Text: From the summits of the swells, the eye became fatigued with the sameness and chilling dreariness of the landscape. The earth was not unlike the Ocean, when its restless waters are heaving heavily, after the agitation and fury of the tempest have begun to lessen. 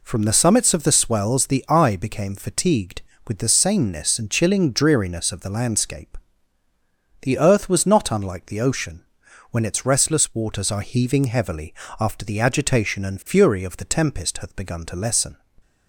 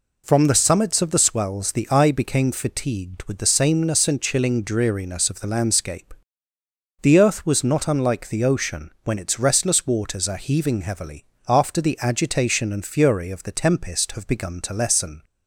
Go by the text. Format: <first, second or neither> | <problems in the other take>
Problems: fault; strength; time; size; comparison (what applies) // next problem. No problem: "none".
second | says "hath" for "have"; at 14.3 s